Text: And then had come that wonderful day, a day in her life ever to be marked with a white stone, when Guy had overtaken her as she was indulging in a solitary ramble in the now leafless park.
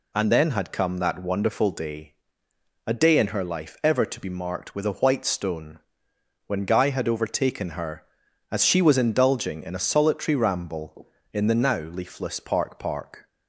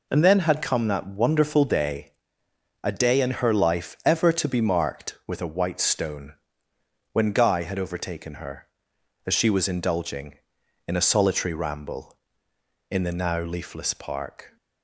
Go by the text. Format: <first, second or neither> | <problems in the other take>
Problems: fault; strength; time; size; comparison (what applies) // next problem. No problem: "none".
second | says "park" twice; at 12.7 s